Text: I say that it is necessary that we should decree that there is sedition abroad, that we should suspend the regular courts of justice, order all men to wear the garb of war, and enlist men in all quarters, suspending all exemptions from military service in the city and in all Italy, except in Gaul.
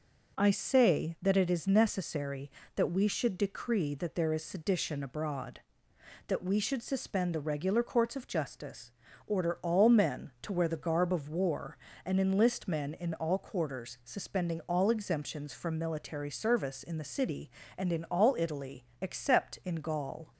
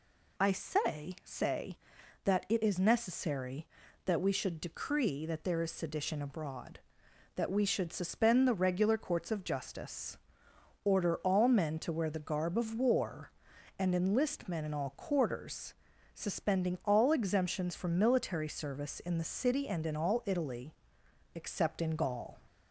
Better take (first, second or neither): first